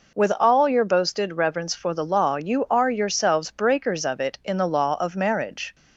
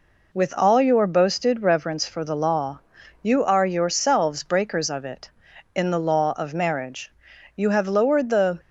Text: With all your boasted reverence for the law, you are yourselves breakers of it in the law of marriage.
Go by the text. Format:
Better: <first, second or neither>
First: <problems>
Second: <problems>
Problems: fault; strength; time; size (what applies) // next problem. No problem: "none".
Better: first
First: none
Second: goes on to say "You have lowered the"; noticeable; from 7.5 s on; 1.0 s long